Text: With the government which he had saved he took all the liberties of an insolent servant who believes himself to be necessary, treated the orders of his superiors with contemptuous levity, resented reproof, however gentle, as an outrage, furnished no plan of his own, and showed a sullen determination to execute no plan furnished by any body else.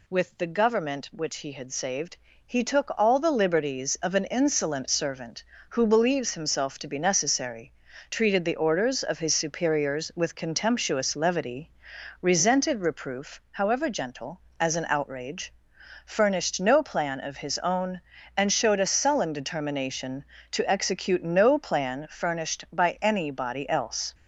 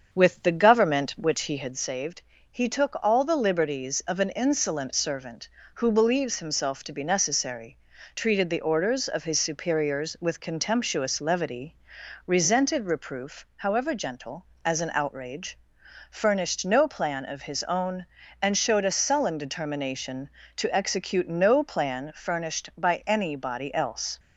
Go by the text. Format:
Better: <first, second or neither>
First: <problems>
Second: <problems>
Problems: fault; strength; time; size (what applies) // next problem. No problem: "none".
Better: first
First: pauses between "saved" and "he"; slight; at 2.1 s; 0.30 s long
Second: starts louder than the rest; until 1.9 s; 7 dB // pauses between "saved" and "he"; slight; at 2.2 s; 0.30 s long